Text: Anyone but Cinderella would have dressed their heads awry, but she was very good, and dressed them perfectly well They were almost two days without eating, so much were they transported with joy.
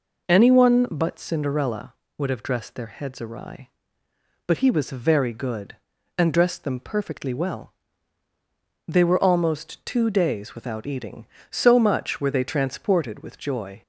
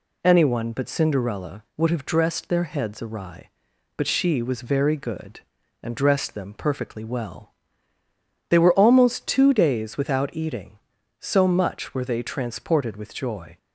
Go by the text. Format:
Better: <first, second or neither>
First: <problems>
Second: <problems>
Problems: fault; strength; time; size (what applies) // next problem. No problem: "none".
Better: second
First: says "he" for "she"; at 4.5 s // pauses between "well" and "They"; at 7.7 s; 1.1 s long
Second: pauses between "well" and "They"; noticeable; at 7.5 s; 0.96 s long